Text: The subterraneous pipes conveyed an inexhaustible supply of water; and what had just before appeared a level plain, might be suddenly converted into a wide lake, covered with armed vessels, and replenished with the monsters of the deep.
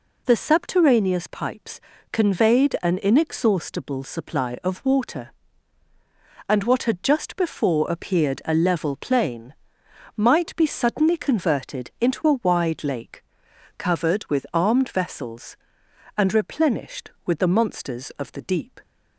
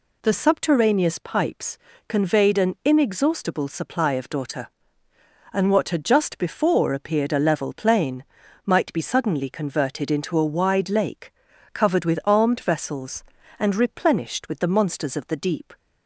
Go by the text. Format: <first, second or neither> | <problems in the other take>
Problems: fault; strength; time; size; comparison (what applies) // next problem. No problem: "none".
first | pauses between "pipes" and "conveyed"; slight; at 1.7 s; 0.28 s long; slight in the first // says "daughter" for "water"; at 4.2 s